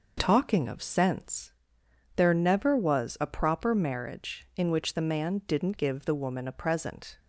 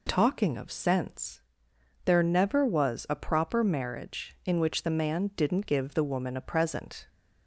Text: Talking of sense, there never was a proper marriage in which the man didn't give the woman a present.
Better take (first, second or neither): second